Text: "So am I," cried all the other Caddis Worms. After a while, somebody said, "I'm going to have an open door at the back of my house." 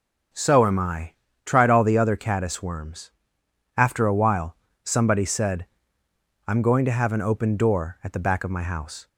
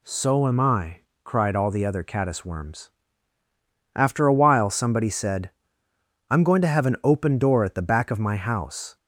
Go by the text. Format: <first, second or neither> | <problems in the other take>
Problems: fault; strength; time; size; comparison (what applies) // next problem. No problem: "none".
second | starts louder than the rest; until 1.6 s; 6.5 dB // says "tried" for "cried"; at 1.4 s